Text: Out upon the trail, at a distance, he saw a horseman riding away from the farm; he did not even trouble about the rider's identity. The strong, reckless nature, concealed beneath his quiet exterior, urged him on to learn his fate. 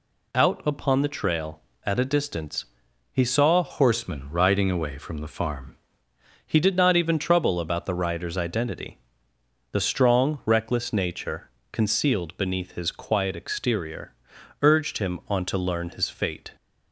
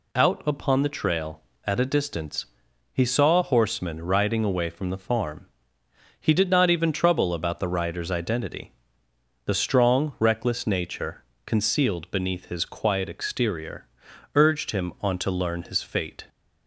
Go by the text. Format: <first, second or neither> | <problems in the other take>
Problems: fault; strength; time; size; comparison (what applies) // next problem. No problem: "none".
second | changes voice from "horseman" to "farm"; from 3.6 to 5.7 s; 2.1 s long